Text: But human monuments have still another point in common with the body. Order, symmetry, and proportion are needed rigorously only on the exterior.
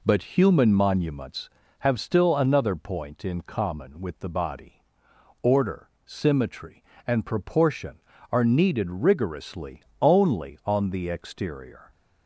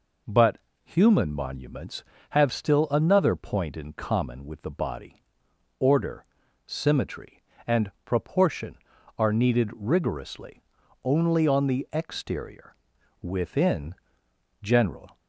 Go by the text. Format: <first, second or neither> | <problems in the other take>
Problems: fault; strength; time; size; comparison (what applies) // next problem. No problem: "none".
first | pauses between "But" and "human"; slight; at 0.5 s; 0.26 s long // pauses between "rigorously" and "only"; at 10.6 s; 0.42 s long; slight in the first // goes on to say "Within general"; strong; from 13.2 s on; 1.9 s long